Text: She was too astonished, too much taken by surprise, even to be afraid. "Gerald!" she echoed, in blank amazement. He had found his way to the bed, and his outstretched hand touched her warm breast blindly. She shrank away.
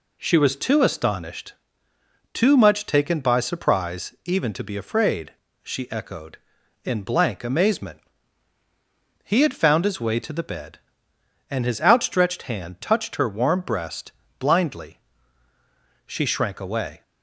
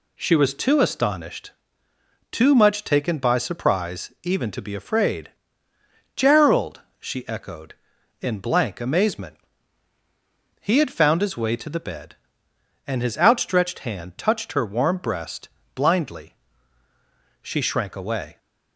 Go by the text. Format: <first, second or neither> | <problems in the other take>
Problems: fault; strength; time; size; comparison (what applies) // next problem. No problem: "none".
second | skips "Gerald"; at 5.4 s // pauses between "breast" and "blindly"; slight; at 14.1 s; 0.26 s long; slight in the second